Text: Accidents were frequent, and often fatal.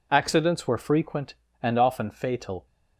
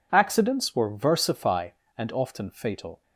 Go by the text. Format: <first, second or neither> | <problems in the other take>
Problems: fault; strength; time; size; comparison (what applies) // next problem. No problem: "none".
first | says "versify" for "frequent"; at 0.8 s